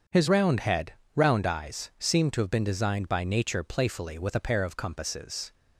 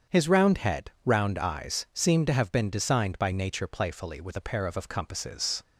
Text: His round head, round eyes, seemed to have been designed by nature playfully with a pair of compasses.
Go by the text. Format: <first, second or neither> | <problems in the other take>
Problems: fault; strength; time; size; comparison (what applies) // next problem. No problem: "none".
first | starts louder than the rest; strong; until 1.2 s; 7.5 dB; also in the first // says "of" twice; at 4.7 s